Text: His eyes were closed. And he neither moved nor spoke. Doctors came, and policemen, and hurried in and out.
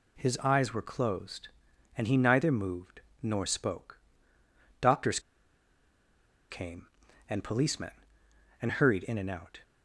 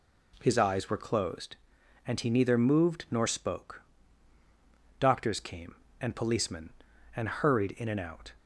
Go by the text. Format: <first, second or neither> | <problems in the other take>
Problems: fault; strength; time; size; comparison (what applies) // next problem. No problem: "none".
second | pauses between "moved" and "nor"; slight; at 3.0 s; 0.22 s long // pauses between "Doctors" and "came"; strong; at 5.1 s; 1.3 s long